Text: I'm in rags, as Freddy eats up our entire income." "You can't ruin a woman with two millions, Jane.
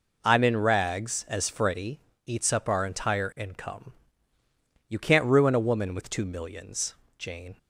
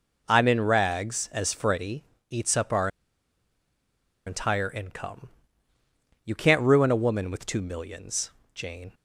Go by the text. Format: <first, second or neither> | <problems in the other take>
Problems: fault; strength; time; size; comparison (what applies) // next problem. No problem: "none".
first | pauses between "Freddy" and "eats"; slight; at 2.0 s; 0.24 s long; slight in the first // pauses between "our" and "entire"; strong; at 2.8 s; 1.3 s long